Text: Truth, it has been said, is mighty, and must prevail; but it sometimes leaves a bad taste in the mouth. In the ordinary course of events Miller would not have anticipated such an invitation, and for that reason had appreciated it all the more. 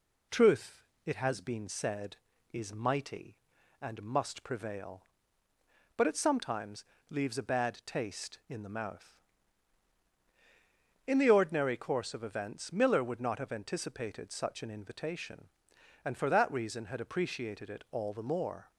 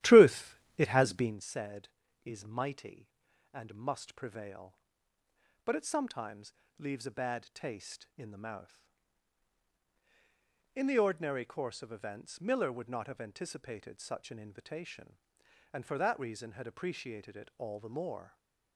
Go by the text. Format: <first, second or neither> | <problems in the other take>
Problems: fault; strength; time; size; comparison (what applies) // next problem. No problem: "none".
first | starts louder than the rest; strong; until 1.4 s; 14 dB // pauses between "sometimes" and "leaves"; slight; at 6.5 s; 0.26 s long; slight in the first // stays silent after the last word; slight; from 18.2 s on; 0.5 s long